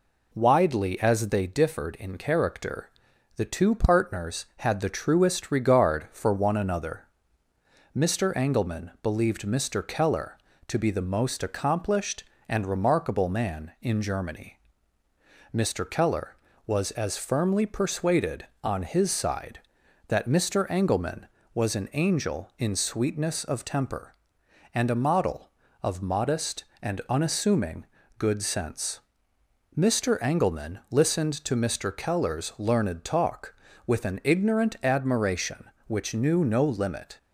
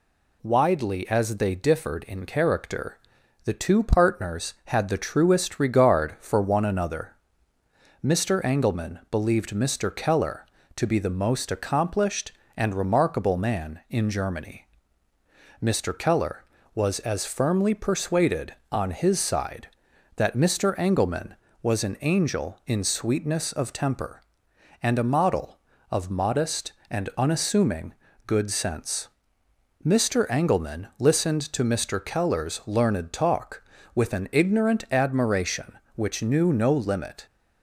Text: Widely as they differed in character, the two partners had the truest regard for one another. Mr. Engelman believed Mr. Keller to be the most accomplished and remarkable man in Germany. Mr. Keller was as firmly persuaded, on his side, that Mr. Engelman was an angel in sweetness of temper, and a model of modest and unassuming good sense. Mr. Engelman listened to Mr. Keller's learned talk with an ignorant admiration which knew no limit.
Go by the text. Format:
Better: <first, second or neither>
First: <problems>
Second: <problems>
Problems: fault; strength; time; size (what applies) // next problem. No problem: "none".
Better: second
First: starts louder than the rest; until 1.4 s; 3.5 dB // pauses between "unassuming" and "good"; slight; at 27.8 s; 0.32 s long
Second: pauses between "unassuming" and "good"; slight; at 27.9 s; 0.32 s long